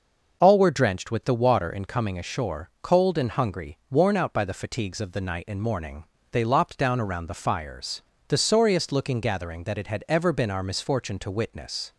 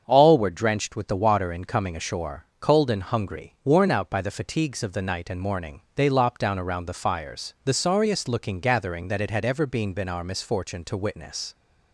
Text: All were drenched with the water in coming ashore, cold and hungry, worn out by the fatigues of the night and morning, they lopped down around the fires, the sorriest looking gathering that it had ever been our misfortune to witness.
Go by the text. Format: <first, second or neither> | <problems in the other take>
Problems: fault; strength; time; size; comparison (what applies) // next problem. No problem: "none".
first | starts louder than the rest; strong; until 1.0 s; 7 dB // says "been" twice; at 9.9 s